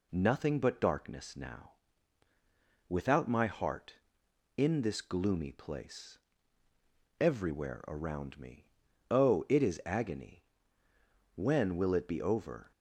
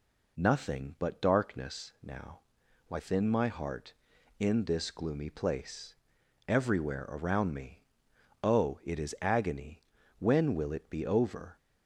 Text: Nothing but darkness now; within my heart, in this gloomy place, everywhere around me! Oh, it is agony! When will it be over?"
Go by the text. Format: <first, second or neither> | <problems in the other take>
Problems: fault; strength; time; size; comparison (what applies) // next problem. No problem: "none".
second | says "without" for "within"; at 2.8 s